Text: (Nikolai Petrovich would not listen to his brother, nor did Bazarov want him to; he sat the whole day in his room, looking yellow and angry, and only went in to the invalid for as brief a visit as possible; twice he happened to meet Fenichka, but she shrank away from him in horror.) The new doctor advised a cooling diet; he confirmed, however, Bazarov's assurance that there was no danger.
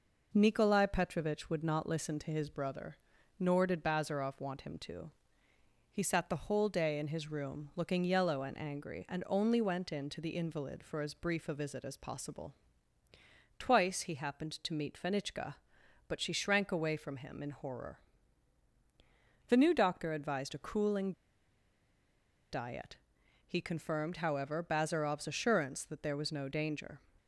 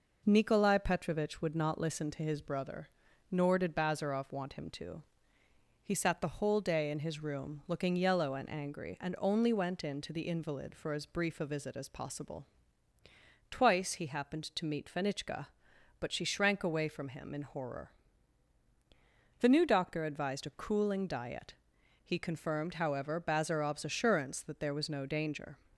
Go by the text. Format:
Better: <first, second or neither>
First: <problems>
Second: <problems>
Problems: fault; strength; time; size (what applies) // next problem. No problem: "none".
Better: second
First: pauses between "cooling" and "diet"; strong; at 21.1 s; 1.4 s long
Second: none